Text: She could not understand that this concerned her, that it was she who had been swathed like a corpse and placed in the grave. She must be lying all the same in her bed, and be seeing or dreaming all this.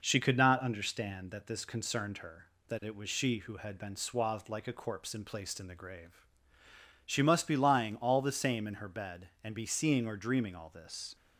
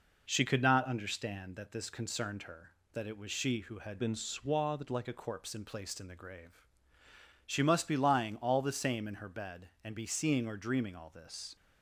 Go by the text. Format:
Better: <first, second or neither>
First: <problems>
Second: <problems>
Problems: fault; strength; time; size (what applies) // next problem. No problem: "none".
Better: first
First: none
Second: changes voice from "been" to "like"; from 3.9 to 5.0 s; 1.1 s long